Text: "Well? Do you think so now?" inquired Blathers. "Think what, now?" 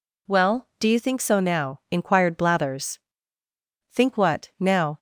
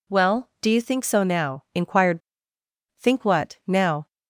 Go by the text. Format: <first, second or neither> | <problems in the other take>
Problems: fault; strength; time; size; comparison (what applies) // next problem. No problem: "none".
first | skips "Blathers"; at 2.5 s